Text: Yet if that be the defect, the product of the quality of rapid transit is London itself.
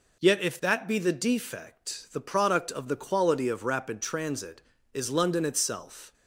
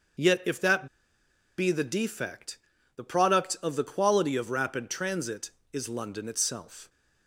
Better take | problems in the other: first | starts louder than the rest; until 1.9 s; 6.5 dB // pauses between "that" and "be"; noticeable; at 0.8 s; 0.69 s long

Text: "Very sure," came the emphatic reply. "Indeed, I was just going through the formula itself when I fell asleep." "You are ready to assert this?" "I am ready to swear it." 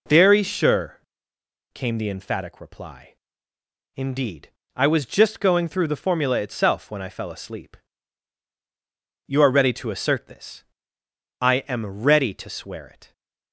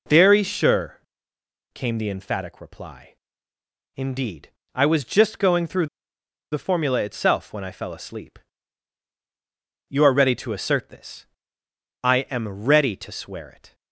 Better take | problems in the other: first | pauses between "through" and "the"; noticeable; at 5.8 s; 0.64 s long

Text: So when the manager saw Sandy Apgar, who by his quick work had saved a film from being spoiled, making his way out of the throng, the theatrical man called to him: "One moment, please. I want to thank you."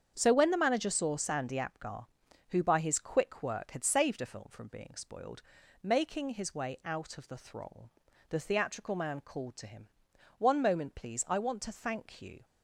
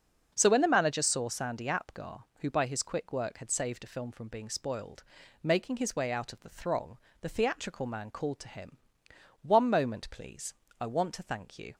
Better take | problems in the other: neither | starts louder than the rest; the same in both

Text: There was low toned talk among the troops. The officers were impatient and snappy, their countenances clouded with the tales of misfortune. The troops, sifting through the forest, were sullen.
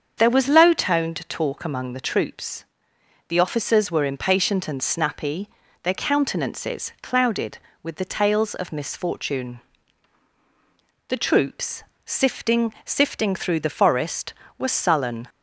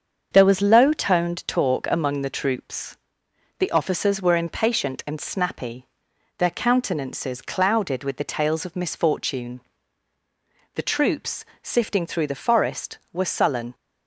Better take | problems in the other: second | starts louder than the rest; strong; until 1.1 s; 7 dB; also in the second // says "sifting" twice; at 12.8 s

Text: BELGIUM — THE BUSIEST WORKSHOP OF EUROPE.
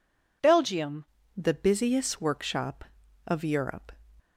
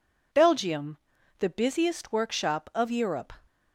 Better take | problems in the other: second | changes voice at "THE"; from 1.3 s on; 2.6 s long

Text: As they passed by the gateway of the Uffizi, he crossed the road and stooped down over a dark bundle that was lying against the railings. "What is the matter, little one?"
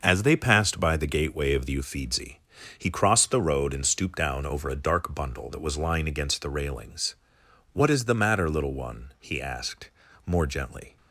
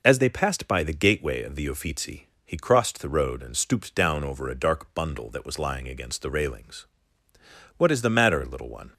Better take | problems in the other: second | starts louder than the rest; noticeable; until 1.0 s; 6 dB // goes on to say "he asked more gently"; strong; from 9.2 s on; 1.7 s long

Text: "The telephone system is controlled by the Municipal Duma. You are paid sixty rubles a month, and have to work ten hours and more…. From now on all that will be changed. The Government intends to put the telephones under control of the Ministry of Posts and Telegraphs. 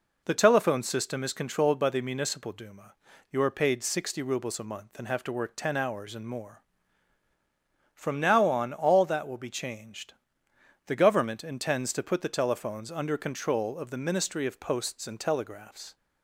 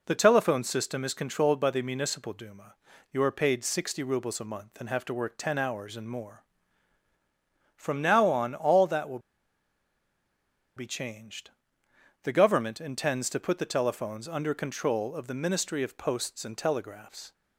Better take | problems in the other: first | pauses between "will" and "be"; strong; at 9.1 s; 1.5 s long

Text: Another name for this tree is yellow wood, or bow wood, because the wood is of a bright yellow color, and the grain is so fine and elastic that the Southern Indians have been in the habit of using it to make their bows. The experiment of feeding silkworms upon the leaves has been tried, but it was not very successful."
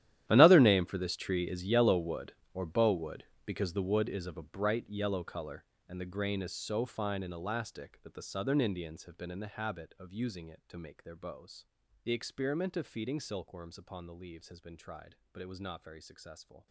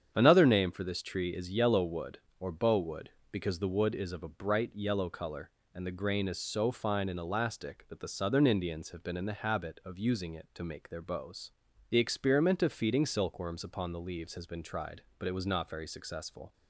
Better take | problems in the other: second | gets quieter; strong; throughout; 18.5 dB // starts louder than the rest; strong; until 1.2 s; 12 dB; strong in the second

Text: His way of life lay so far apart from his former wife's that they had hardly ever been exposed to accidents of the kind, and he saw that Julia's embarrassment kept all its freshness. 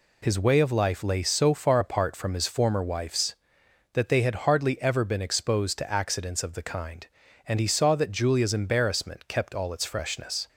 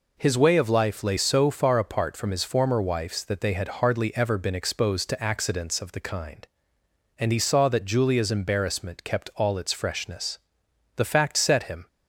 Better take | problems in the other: first | goes on to say "The fact set him"; noticeable; from 10.9 s on; 0.92 s long

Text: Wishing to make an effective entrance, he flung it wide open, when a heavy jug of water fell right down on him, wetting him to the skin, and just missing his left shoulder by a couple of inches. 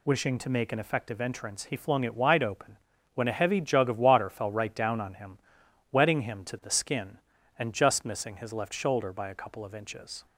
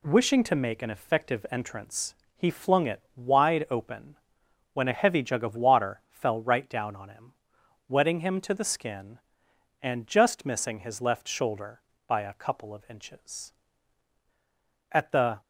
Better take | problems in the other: first | goes on to say "At the"; from 14.9 s on; 0.50 s long

